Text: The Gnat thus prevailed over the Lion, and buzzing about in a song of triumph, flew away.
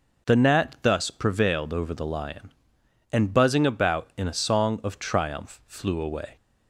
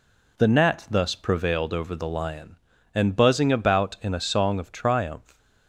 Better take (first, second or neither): first